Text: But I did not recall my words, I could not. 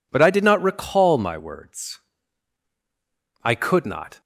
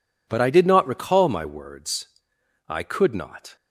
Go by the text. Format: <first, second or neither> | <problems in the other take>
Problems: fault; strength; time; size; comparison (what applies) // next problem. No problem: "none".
neither | none